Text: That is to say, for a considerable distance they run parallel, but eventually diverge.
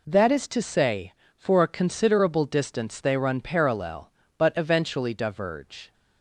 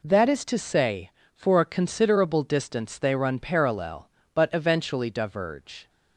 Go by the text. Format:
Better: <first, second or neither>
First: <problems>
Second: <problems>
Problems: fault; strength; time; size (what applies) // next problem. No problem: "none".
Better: neither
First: none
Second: none